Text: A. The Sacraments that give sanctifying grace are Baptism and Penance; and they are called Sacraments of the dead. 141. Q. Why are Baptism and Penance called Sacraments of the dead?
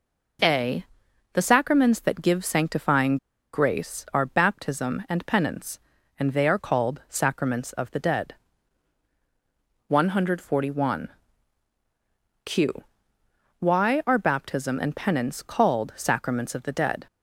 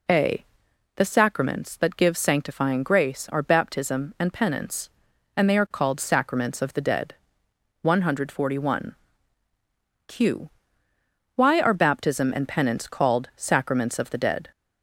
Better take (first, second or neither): second